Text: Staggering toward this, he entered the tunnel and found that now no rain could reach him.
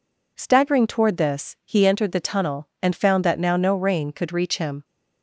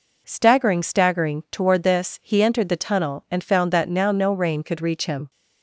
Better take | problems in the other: first | says "Staggering" twice; at 0.8 s

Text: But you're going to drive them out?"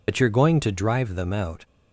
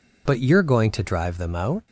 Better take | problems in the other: second | loses the start of "But"; at 0.0 s; 60 ms

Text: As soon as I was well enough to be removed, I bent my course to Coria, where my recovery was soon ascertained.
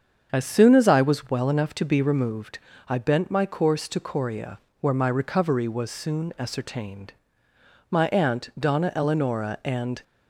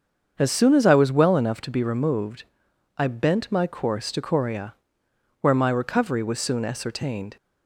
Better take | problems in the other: second | starts louder than the rest; until 1.3 s; 7 dB; also in the second // goes on to say "My aunt Donna Eleonora and"; strong; from 7.8 s on; 2.1 s long

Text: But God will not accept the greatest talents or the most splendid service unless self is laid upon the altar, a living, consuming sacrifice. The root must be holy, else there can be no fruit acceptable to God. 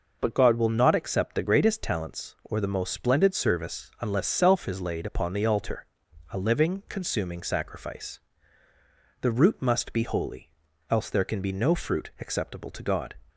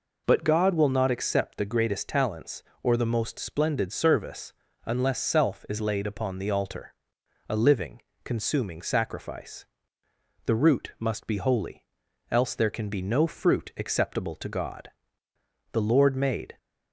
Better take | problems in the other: first | pauses between "service" and "unless"; slight; at 4.5 s; 0.34 s long // goes on to say "The Lord made"; noticeable; from 15.7 s on; 0.86 s long

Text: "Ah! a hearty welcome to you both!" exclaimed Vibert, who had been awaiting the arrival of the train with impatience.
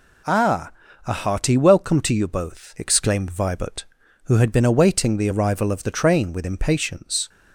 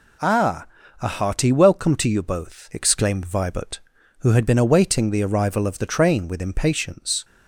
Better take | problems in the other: neither | none

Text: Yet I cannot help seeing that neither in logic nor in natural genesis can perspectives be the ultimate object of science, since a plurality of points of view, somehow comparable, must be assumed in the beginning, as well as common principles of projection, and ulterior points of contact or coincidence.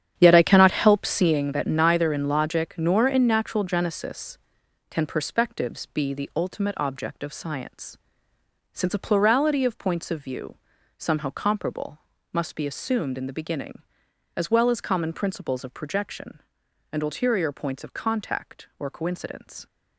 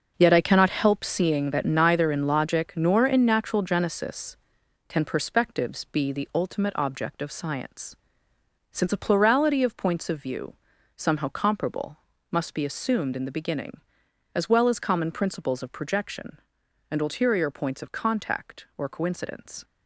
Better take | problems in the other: second | starts louder than the rest; strong; until 1.5 s; 9 dB

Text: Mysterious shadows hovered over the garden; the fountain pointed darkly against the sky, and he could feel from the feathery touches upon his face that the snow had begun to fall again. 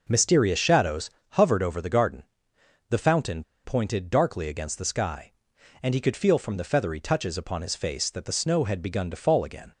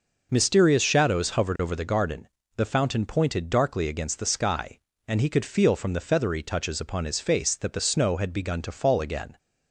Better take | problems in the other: second | pauses between "shadows" and "hovered"; slight; at 1.0 s; 0.22 s long // pauses between "fountain" and "pointed"; slight; at 3.4 s; 0.20 s long

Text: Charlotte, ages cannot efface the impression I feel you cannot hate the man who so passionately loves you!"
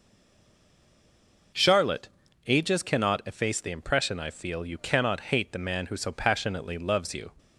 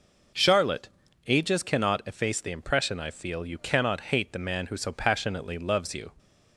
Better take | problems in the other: second | stays silent before the first word; noticeable; until 1.5 s; 1.5 s long

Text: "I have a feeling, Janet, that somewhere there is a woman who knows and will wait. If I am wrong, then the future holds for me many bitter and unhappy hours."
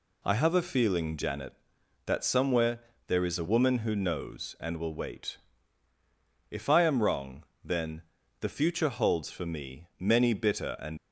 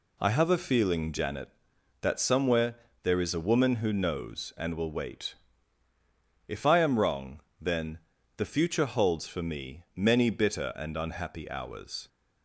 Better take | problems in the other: second | pauses between "somewhere" and "there"; slight; at 2.7 s; 0.28 s long; slight in the second // pauses between "then" and "the"; slight; at 8.0 s; 0.36 s long; slight in the second // stops before "unhappy hours"; at 10.9 s

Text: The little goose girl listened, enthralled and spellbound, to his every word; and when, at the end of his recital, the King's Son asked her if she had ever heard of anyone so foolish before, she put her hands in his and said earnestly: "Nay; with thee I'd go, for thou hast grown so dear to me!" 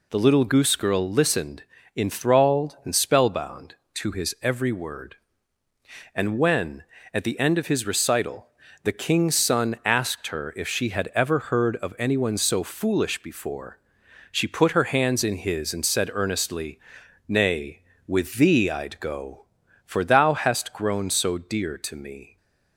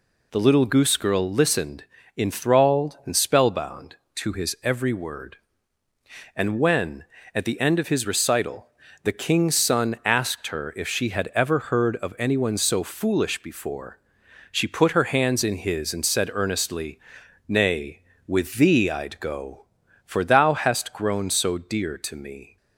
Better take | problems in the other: neither | none

